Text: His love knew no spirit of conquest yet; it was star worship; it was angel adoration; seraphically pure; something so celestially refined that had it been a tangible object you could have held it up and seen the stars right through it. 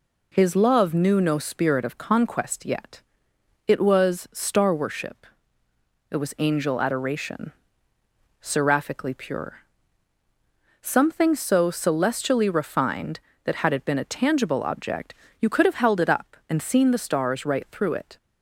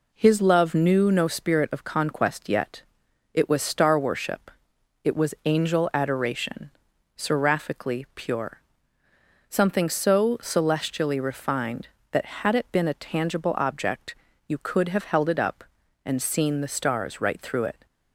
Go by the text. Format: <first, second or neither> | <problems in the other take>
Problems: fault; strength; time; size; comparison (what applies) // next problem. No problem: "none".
neither | pauses between "object" and "you"; slight; the same in both